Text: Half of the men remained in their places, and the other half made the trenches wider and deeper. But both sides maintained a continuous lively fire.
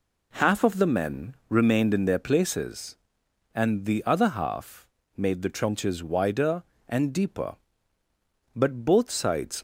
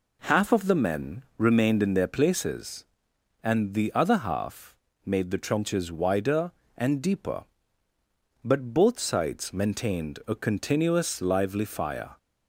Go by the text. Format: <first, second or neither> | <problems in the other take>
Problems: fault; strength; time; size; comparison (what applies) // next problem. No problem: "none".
second | pauses between "half" and "made"; slight; at 4.8 s; 0.30 s long; slight in the second // stops before "maintained a continuous lively fire"; at 9.5 s